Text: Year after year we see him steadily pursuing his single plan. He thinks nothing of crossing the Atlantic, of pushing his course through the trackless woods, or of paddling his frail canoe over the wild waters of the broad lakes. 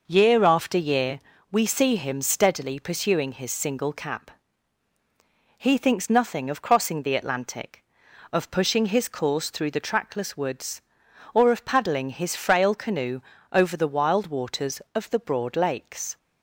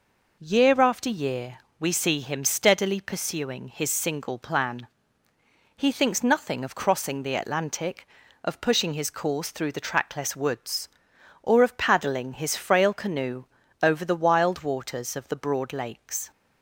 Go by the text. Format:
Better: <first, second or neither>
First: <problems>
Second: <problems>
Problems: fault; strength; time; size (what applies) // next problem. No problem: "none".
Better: second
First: pauses between "year" and "we"; slight; at 1.2 s; 0.28 s long // says "cap" for "plan"; at 3.9 s // pauses between "canoe" and "over"; slight; at 13.2 s; 0.32 s long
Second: pauses between "year" and "we"; slight; at 1.5 s; 0.22 s long // pauses between "canoe" and "over"; slight; at 13.4 s; 0.36 s long